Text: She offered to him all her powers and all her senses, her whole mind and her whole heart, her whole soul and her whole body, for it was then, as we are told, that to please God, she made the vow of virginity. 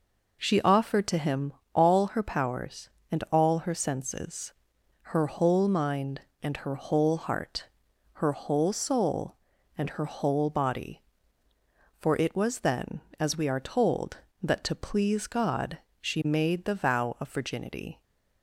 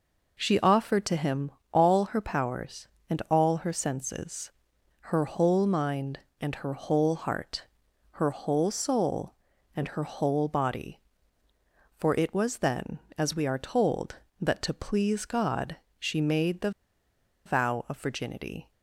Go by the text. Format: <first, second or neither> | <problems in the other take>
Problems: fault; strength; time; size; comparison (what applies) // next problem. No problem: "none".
first | pauses between "him" and "all"; slight; at 1.4 s; 0.22 s long; slight in the first // pauses between "the" and "vow"; noticeable; at 16.6 s; 0.75 s long